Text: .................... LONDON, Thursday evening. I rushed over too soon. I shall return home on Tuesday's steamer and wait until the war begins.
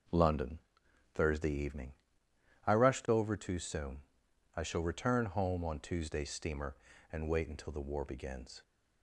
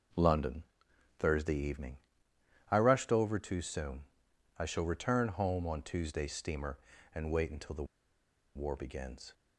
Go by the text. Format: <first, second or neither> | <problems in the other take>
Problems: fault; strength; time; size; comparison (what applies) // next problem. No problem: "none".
first | pauses between "the" and "war"; noticeable; at 7.8 s; 0.71 s long